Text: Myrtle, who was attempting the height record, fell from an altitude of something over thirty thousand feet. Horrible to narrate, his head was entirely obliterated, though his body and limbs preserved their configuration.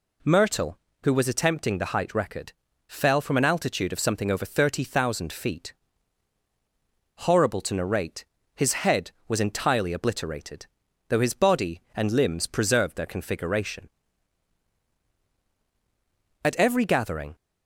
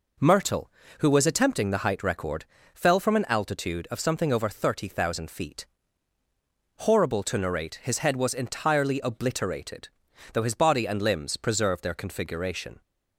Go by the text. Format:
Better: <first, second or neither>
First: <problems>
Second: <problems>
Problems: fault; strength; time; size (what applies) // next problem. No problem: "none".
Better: second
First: goes on to say "At every gathering"; noticeable; from 16.4 s on; 0.92 s long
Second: none